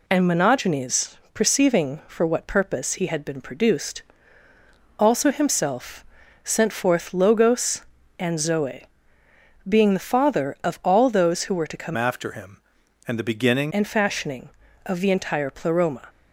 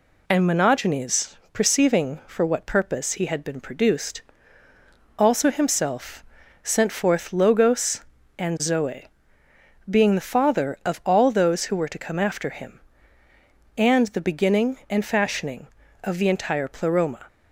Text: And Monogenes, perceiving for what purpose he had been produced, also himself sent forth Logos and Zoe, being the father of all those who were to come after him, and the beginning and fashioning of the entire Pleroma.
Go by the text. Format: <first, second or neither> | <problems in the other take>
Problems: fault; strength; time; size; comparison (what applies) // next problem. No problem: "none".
second | pauses between "himself" and "sent"; at 6.0 s; 0.40 s long; also in the second // changes voice from "after" to "beginning"; from 11.9 to 13.7 s; 1.8 s long